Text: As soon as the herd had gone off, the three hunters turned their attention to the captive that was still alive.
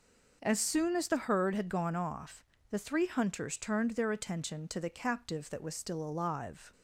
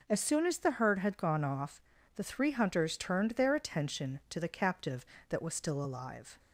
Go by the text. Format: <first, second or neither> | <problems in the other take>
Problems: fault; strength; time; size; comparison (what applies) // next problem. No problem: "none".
neither | none